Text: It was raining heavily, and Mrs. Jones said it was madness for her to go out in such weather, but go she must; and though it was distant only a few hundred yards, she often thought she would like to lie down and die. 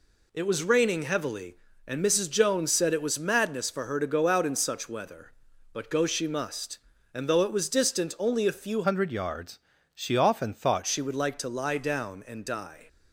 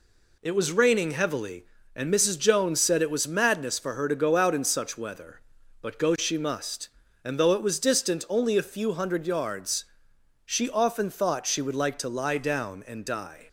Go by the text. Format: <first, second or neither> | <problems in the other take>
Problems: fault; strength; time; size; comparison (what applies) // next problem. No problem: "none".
second | changes voice from "hundred" to "thought"; from 8.8 to 10.8 s; 2.0 s long